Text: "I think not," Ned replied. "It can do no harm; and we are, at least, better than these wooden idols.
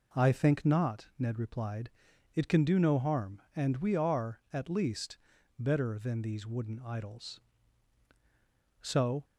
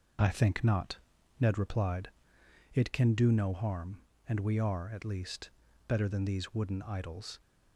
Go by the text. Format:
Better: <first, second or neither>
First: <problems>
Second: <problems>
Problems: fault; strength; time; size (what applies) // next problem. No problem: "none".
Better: second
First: goes on to say "So"; slight; from 8.8 s on; 0.42 s long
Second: none